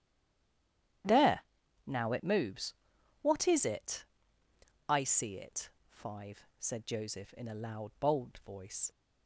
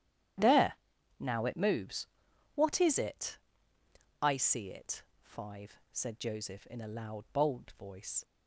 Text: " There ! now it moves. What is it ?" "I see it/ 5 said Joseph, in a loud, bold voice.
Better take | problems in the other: second | stays silent before the first word; until 1.0 s; 1.0 s long // starts louder than the rest; strong; until 2.4 s; 11 dB; strong in the second

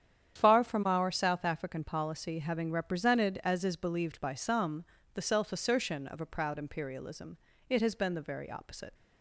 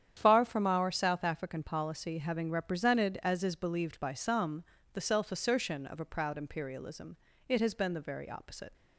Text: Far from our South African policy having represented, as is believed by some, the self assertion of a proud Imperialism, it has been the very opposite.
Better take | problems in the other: neither | starts louder than the rest; strong; the same in both

